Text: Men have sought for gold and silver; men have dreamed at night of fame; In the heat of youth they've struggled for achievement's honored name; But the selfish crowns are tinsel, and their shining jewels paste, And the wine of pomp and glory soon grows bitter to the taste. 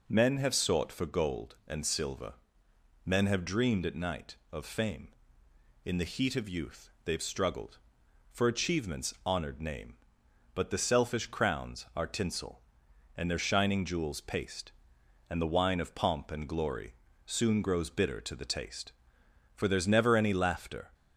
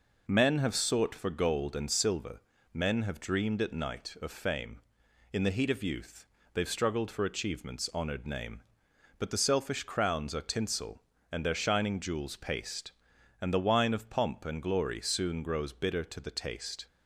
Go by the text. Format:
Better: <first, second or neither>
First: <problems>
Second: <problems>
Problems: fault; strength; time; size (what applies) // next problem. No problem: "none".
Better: second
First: pauses between "youth" and "they've"; slight; at 6.8 s; 0.16 s long // pauses between "glory" and "soon"; slight; at 16.9 s; 0.28 s long // goes on to say "For there's never any laughter"; from 19.5 s on; 1.3 s long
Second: pauses between "youth" and "they've"; slight; at 6.2 s; 0.26 s long